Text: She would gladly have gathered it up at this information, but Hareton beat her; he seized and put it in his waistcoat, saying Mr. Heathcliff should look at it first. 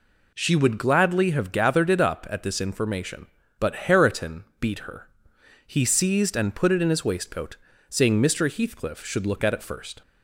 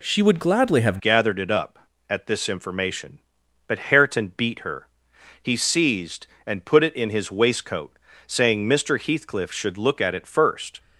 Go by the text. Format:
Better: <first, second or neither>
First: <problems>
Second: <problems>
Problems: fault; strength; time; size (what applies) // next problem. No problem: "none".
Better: first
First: none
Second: changes voice at "gathered"; from 0.9 s on; 9.8 s long